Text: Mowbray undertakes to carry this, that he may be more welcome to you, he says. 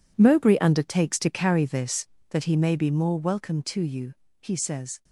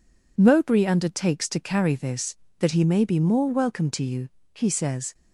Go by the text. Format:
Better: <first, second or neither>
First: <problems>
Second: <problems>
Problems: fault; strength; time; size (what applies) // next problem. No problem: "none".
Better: second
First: gets quieter; strong; throughout; 13.5 dB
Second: none